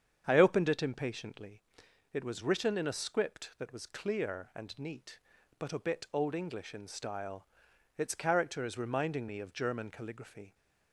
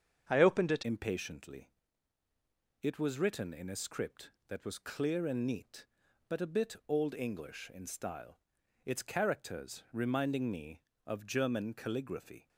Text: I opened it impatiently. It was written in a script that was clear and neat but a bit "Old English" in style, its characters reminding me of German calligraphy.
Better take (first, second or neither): first